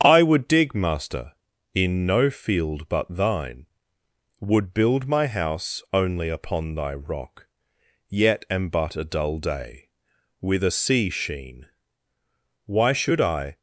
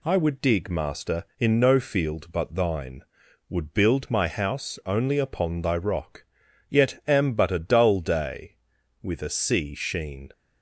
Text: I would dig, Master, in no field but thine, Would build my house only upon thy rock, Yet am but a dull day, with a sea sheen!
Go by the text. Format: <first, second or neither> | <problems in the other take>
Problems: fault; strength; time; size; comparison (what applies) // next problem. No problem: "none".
second | starts louder than the rest; strong; until 1.0 s; 8 dB // goes on to say "Why should I"; noticeable; from 12.6 s on; 0.92 s long